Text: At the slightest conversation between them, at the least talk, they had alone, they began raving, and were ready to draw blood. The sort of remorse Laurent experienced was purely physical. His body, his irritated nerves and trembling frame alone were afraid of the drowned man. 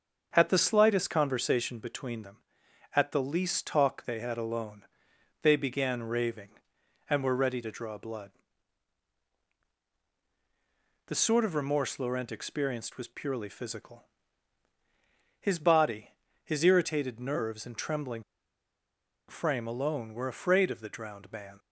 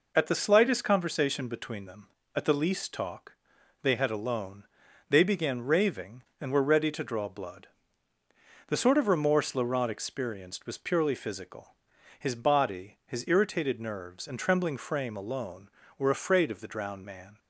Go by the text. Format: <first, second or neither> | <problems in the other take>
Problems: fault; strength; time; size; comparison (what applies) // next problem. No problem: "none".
second | starts louder than the rest; until 1.3 s; 7 dB // pauses between "trembling" and "frame"; at 18.2 s; 1.0 s long